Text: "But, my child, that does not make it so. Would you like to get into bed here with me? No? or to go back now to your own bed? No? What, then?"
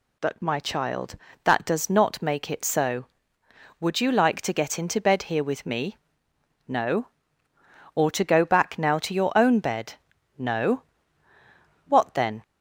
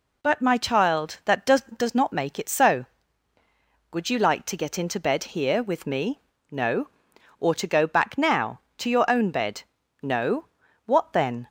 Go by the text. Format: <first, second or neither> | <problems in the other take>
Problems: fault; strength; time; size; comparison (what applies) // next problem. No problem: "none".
first | says "does" twice; at 1.7 s